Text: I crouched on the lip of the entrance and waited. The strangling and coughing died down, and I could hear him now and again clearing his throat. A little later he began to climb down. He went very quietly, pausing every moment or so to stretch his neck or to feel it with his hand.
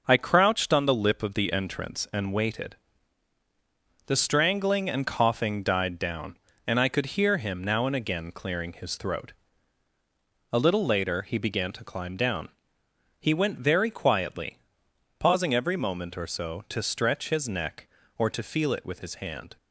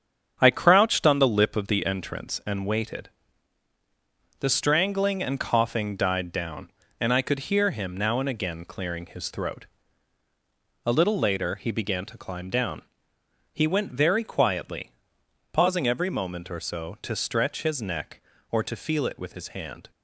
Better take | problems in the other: first | starts louder than the rest; strong; until 1.9 s; 8 dB

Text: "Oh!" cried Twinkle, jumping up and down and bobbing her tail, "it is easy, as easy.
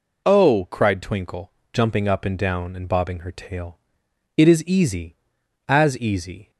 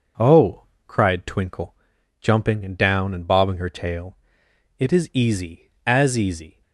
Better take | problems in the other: first | skips "up"; at 2.6 s

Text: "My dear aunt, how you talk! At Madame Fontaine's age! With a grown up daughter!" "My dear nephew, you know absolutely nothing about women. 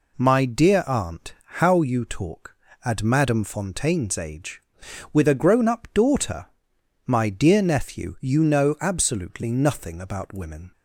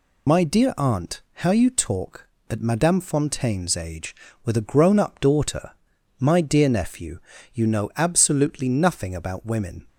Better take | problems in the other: first | loses the start of "My"; at 0.2 s; 40 ms

